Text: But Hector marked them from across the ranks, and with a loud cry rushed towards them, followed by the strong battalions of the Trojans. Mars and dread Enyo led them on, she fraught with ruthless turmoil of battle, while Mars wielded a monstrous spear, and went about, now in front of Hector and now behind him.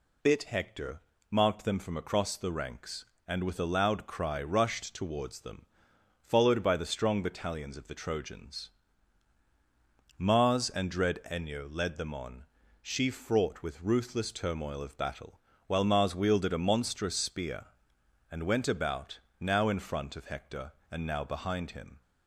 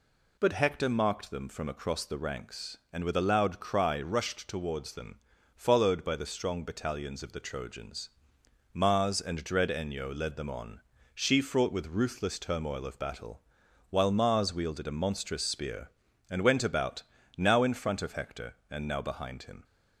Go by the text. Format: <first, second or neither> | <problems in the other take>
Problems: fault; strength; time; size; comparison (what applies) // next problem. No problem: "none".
second | says "Bit" for "But"; at 0.2 s // pauses between "Hector" and "marked"; slight; at 1.0 s; 0.30 s long